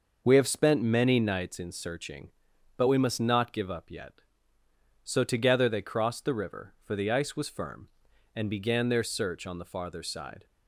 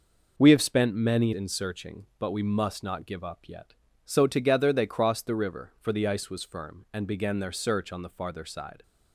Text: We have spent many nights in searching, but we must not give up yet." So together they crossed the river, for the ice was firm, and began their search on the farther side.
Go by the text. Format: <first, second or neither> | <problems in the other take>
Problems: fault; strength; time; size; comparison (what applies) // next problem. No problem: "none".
first | skips "nights"; at 1.3 s